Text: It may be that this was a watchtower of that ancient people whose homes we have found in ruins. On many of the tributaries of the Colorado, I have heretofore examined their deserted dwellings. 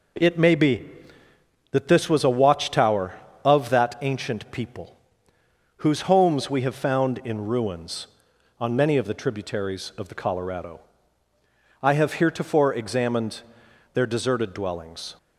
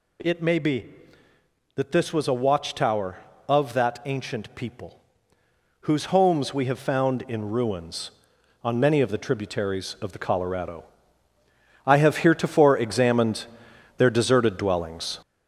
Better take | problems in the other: first | gets louder; noticeable; throughout; 5.5 dB // pauses between "people" and "whose"; noticeable; at 4.9 s; 0.82 s long; noticeable in the first // pauses between "examined" and "their"; noticeable; at 13.4 s; 0.52 s long; noticeable in the first

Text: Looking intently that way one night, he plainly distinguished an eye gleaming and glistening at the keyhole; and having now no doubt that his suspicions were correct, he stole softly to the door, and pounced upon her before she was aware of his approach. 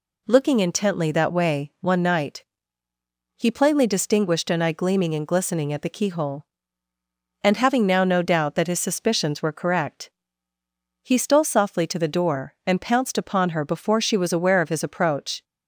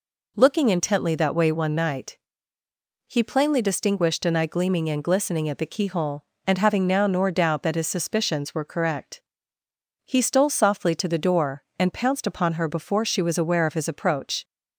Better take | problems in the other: first | says "nor" for "no"; at 7.0 s

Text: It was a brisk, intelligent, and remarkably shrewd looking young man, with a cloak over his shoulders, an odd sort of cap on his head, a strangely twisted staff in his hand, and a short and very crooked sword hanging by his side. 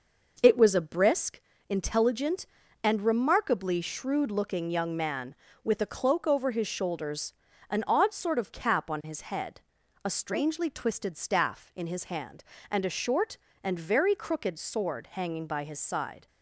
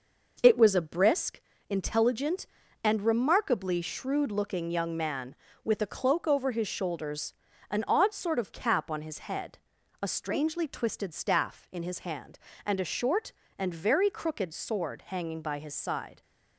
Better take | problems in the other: neither | none

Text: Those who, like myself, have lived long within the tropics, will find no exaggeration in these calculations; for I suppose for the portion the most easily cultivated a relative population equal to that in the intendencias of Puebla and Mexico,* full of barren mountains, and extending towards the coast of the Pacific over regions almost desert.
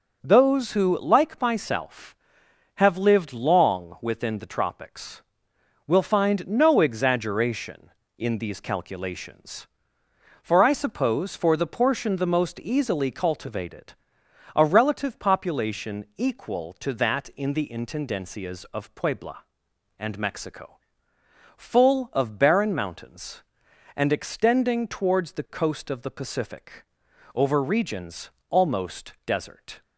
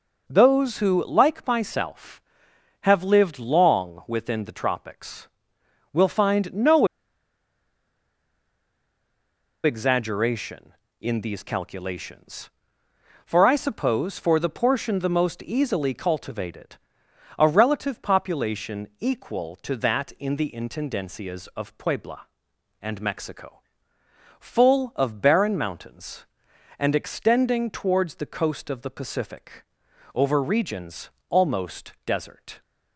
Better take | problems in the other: first | pauses between "no" and "exaggeration"; strong; at 6.8 s; 2.7 s long // pauses between "cultivated" and "a"; noticeable; at 16.7 s; 0.60 s long; noticeable in the first // pauses between "Pacific" and "over"; noticeable; at 29.6 s; 0.50 s long; noticeable in the first // pauses between "regions" and "almost"; slight; at 31.0 s; 0.20 s long; slight in the first

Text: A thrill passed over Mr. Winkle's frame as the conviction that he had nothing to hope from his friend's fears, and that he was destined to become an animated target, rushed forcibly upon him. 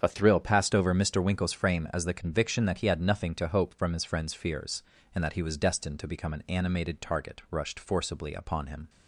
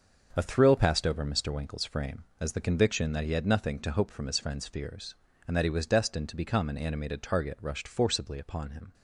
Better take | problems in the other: neither | starts louder than the rest; the same in both

